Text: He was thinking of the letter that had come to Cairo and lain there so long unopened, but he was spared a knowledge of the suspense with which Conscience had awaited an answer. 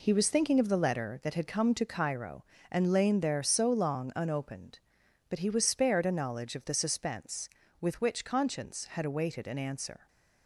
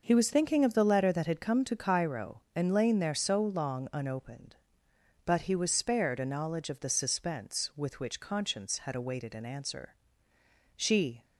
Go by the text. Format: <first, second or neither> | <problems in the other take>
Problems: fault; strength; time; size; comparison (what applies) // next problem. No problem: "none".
first | goes on to say "She"; slight; from 10.7 s on; 0.48 s long